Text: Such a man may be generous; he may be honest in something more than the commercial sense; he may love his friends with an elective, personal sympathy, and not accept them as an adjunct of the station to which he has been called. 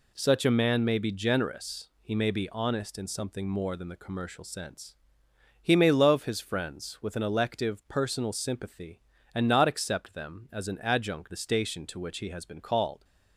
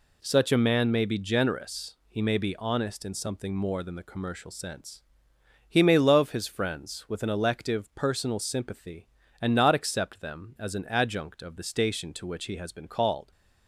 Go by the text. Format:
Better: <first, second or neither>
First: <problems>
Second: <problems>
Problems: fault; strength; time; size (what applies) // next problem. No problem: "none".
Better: second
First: skips "of"; at 11.3 s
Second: none